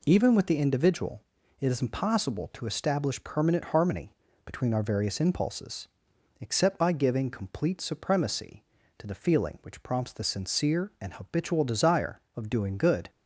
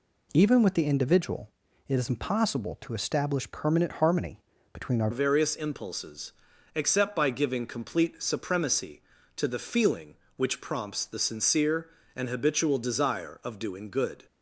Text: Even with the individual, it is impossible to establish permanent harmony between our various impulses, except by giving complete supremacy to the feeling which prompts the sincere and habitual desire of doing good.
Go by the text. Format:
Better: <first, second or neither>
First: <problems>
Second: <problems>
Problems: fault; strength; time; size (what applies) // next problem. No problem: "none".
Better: first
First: pauses between "harmony" and "between"; slight; at 4.1 s; 0.34 s long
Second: pauses between "harmony" and "between"; slight; at 4.3 s; 0.34 s long // changes voice at "various"; from 5.1 s on; 9.1 s long